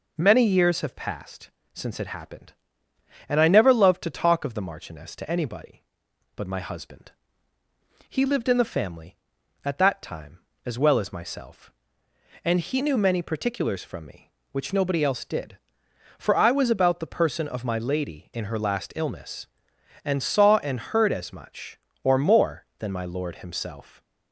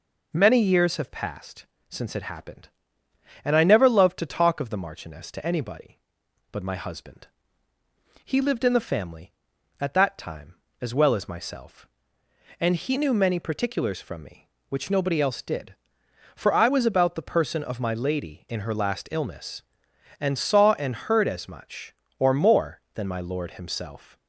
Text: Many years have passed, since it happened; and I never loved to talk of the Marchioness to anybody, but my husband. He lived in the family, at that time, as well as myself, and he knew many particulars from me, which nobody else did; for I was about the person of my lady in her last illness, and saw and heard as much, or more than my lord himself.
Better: neither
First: none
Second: none

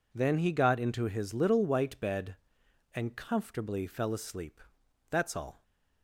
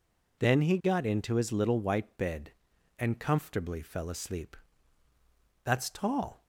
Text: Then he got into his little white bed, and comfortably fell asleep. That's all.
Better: first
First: none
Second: says "tall" for "all"; at 5.8 s

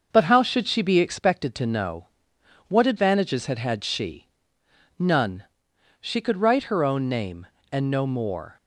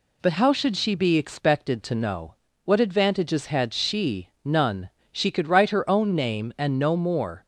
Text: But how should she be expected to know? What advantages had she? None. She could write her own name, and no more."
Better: second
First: starts louder than the rest; until 1.1 s; 6.5 dB // says "had" twice; at 3.5 s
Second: none

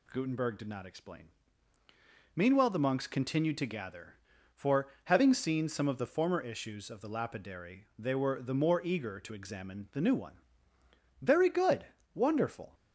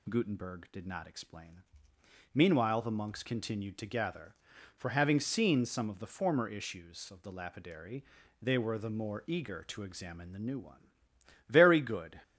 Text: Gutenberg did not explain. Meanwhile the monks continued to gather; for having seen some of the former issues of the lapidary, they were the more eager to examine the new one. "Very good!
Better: second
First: pauses between "for" and "having"; slight; at 4.8 s; 0.18 s long // goes on to say "wonderful"; from 12.1 s on; 0.60 s long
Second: none

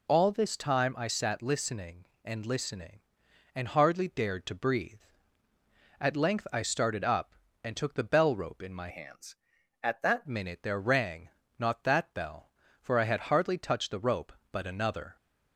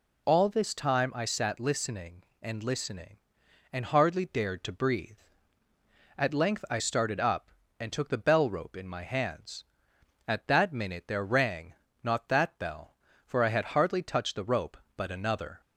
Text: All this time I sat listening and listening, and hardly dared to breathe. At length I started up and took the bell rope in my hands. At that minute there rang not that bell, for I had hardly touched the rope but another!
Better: second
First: changes voice from "hands" to "that"; from 8.8 to 10.2 s; 1.4 s long // pauses between "rang" and "not"; slight; at 11.2 s; 0.28 s long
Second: pauses between "rang" and "not"; slight; at 11.7 s; 0.28 s long

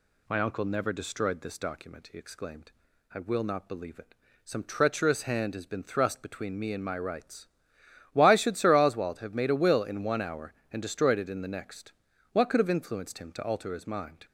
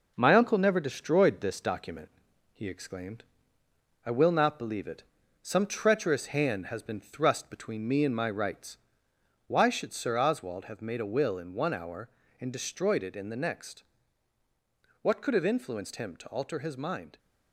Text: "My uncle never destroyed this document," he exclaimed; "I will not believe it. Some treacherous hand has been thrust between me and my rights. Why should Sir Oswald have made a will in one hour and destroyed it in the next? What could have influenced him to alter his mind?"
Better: first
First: none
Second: gets quieter; noticeable; throughout; 4 dB

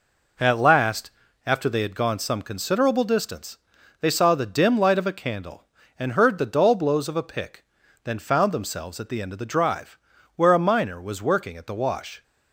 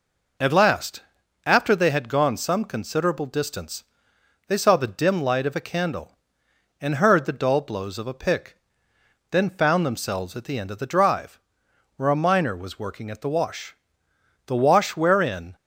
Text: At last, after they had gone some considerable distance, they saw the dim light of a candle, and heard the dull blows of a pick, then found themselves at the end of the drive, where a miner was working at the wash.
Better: first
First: none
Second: goes on to say "The wash wherein"; noticeable; from 14.4 s on; 1.0 s long

